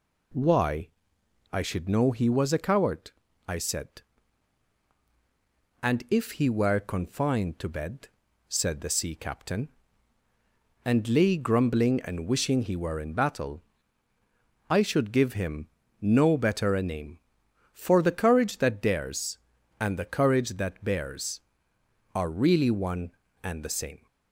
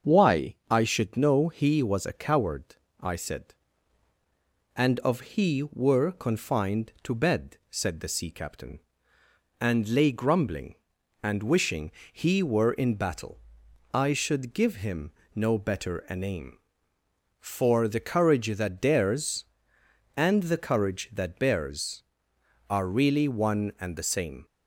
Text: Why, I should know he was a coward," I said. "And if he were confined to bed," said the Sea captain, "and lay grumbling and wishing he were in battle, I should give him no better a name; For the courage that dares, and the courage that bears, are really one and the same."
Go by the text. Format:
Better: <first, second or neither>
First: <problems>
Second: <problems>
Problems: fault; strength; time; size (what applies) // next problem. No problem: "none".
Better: first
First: pauses between "him" and "no"; slight; at 15.6 s; 0.32 s long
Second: starts louder than the rest; until 1.2 s; 6.5 dB // says "of" for "if"; at 4.9 s // pauses between "wishing" and "he"; slight; at 11.9 s; 0.22 s long // pauses between "him" and "no"; slight; at 15.1 s; 0.24 s long